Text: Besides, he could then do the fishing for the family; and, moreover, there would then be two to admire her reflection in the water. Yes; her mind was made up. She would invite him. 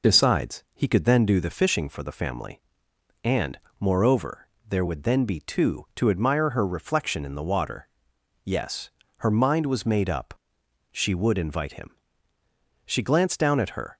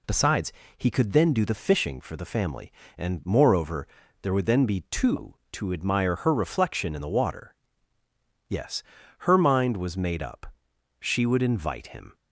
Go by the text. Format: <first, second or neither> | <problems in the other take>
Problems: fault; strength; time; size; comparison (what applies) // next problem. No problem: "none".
second | goes on to say "She glanced down at her"; noticeable; from 12.8 s on; 1.1 s long